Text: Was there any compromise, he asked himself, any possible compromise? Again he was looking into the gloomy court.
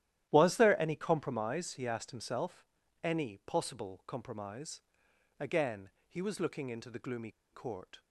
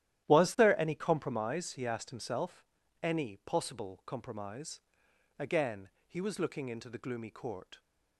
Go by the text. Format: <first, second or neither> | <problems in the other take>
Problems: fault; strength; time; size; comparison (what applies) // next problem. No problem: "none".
second | starts louder than the rest; strong; until 1.3 s; 12.5 dB; strong in the second // pauses between "Again" and "he"; slight; at 5.8 s; 0.16 s long; slight in the second // pauses between "gloomy" and "court"; slight; at 7.2 s; 0.22 s long